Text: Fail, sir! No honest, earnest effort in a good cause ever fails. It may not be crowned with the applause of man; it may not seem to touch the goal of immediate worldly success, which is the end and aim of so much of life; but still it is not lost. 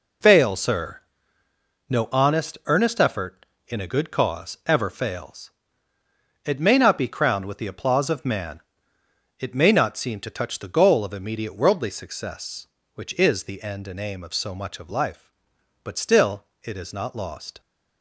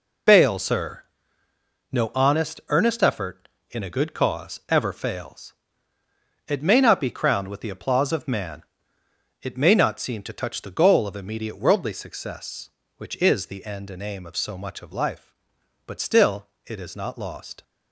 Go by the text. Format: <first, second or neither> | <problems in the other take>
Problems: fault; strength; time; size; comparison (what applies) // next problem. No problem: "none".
first | loses the start of "Fail"; at 0.2 s; 25 ms // pauses between "still" and "it"; slight; at 16.4 s; 0.18 s long; slight in the first